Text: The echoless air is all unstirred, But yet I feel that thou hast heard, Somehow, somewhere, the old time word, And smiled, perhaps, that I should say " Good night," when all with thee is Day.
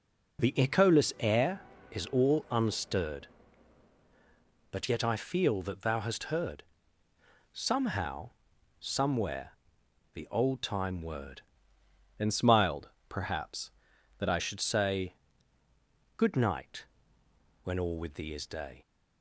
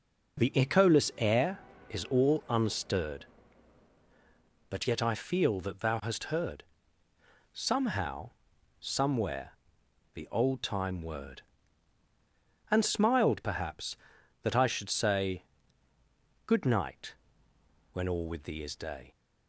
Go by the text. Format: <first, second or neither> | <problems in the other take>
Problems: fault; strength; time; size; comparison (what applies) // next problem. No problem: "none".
second | changes voice from "And" to "I"; from 12.1 to 14.4 s; 2.3 s long